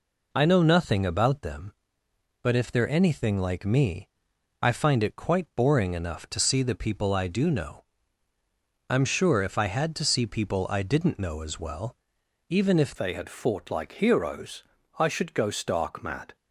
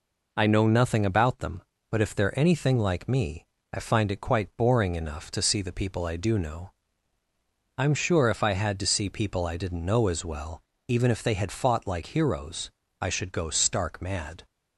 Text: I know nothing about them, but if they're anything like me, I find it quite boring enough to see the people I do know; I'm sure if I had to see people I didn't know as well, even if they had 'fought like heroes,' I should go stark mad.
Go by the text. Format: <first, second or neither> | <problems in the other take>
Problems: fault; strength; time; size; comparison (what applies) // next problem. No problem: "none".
second | changes voice at "they"; from 12.9 s on; 3.4 s long